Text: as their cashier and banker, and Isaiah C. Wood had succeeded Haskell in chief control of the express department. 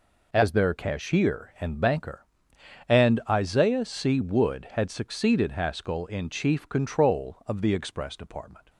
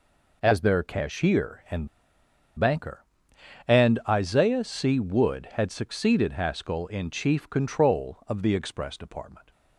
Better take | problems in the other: first | pauses between "and" and "banker"; noticeable; at 1.8 s; 0.70 s long

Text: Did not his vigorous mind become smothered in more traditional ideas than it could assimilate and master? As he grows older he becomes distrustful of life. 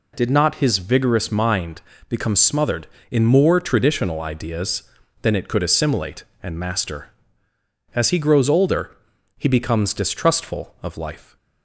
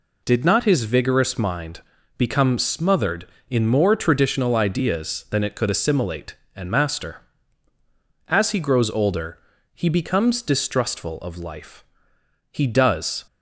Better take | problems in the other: first | pauses between "mind" and "become"; slight; at 1.8 s; 0.36 s long; slight in the first // pauses between "older" and "he"; slight; at 9.3 s; 0.34 s long; also in the first // goes on to say "He does"; noticeable; from 12.5 s on; 0.68 s long

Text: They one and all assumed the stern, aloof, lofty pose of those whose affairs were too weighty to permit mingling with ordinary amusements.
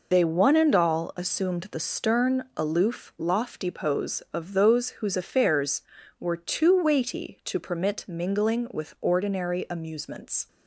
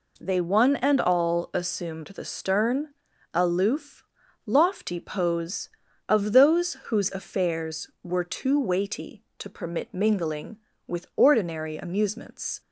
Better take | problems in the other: second | loses the start of "They"; at 0.1 s; 50 ms

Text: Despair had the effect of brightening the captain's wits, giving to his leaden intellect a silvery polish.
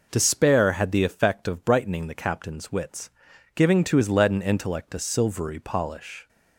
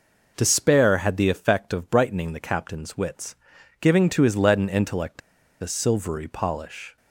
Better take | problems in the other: first | pauses between "intellect" and "a"; at 5.2 s; 0.42 s long

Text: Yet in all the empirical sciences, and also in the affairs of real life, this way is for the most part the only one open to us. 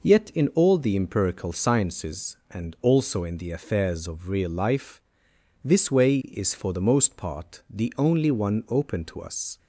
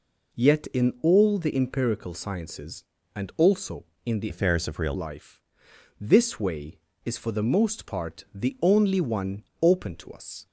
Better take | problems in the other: first | changes voice from "affairs" to "real"; from 4.2 to 4.9 s; 0.7 s long // pauses between "one" and "open"; slight; at 9.4 s; 0.18 s long

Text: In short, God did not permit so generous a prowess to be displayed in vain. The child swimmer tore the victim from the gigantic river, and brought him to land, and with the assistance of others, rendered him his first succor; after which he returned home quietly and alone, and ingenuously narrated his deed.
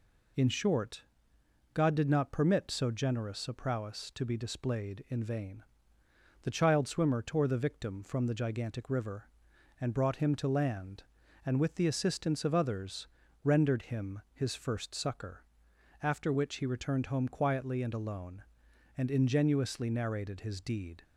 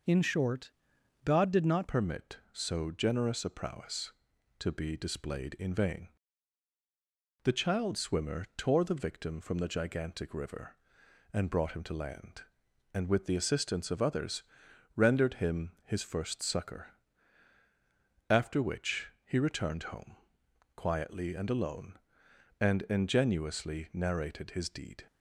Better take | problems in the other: first | changes voice at "permit"; from 1.8 s on; 23.2 s long // pauses between "home" and "quietly"; noticeable; at 20.1 s; 0.62 s long

